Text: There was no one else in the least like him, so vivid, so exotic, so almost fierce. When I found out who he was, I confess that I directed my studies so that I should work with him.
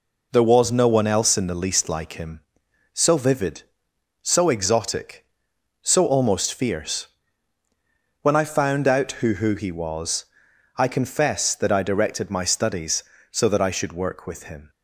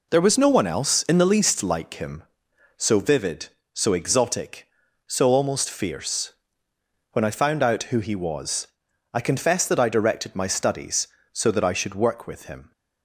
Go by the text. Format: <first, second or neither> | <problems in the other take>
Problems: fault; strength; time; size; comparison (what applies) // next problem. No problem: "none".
second | says "who" twice; at 9.3 s